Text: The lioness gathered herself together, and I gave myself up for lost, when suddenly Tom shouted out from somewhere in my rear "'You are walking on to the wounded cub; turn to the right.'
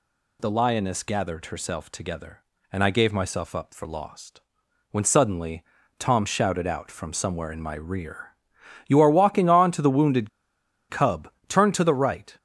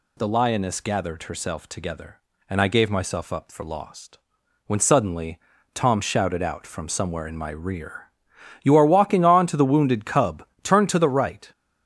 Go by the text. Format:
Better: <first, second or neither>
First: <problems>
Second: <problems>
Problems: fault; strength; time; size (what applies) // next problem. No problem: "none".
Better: second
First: pauses between "suddenly" and "Tom"; slight; at 5.6 s; 0.36 s long // pauses between "rear" and "You"; noticeable; at 8.2 s; 0.58 s long // pauses between "wounded" and "cub"; noticeable; at 10.2 s; 0.61 s long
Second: pauses between "suddenly" and "Tom"; slight; at 5.3 s; 0.36 s long // pauses between "rear" and "You"; noticeable; at 8.0 s; 0.58 s long